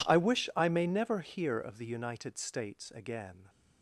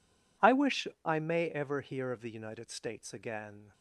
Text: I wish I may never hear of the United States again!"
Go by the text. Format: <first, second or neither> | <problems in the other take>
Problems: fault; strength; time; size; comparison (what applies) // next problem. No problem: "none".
first | pauses between "wish" and "I"; slight; at 0.8 s; 0.18 s long // says "ever" for "never"; at 1.4 s